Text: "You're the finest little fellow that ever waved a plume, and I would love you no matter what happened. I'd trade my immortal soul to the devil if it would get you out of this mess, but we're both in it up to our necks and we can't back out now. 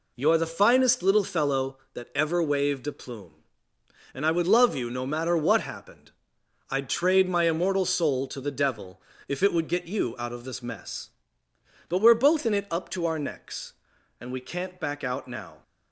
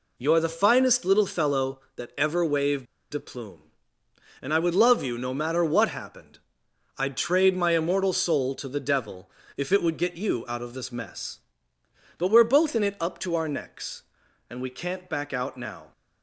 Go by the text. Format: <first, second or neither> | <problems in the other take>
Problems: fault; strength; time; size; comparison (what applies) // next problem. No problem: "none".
first | pauses between "waved" and "a"; slight; at 2.8 s; 0.28 s long // pauses between "devil" and "if"; slight; at 9.2 s; 0.26 s long; slight in the first